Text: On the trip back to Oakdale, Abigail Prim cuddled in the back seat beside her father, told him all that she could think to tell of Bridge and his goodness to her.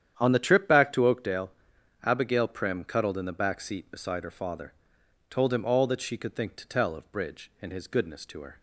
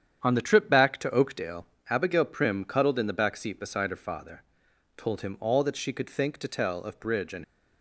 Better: first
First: starts louder than the rest; strong; until 1.1 s; 9.5 dB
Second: starts louder than the rest; strong; until 1.2 s; 9 dB // stops before "his goodness to her"; at 7.4 s

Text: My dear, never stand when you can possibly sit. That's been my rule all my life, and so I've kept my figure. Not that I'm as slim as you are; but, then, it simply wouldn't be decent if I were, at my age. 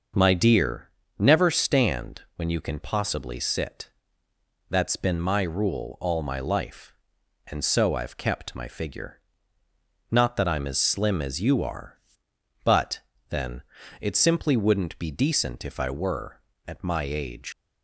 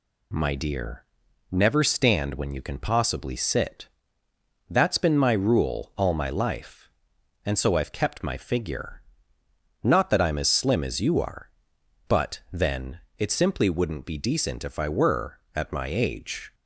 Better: second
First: starts louder than the rest; noticeable; until 1.4 s; 6 dB // pauses between "stand" and "when"; slight; at 2.2 s; 0.16 s long // leaves "age" unfinished; at 17.5 s; 120 ms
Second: none

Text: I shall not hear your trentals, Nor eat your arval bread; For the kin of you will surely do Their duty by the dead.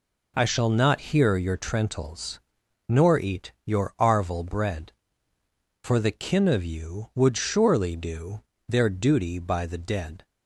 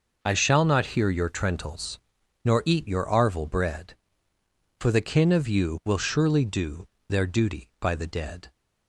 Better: second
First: says "would" for "will"; at 7.1 s // pauses between "do" and "Their"; slight; at 8.4 s; 0.24 s long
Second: pauses between "do" and "Their"; slight; at 6.8 s; 0.22 s long

